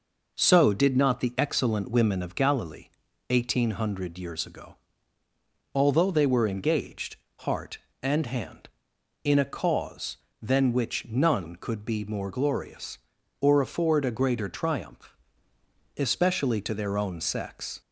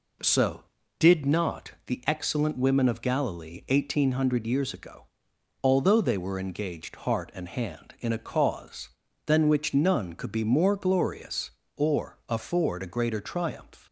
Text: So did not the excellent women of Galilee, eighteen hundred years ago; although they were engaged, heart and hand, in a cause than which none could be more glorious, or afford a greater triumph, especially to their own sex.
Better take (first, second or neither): first